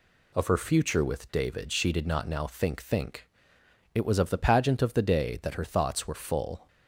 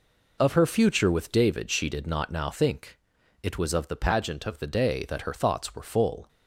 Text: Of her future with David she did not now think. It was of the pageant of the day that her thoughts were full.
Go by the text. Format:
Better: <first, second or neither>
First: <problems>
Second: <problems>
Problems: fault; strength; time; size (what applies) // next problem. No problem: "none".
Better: second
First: says "think" twice; at 2.8 s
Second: none